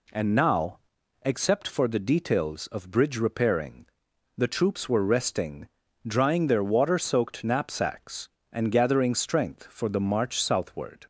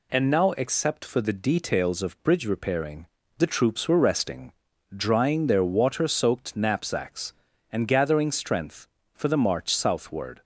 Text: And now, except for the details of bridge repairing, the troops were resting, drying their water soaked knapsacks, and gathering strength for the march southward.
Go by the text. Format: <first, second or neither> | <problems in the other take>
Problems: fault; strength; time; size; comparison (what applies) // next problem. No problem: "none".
neither | none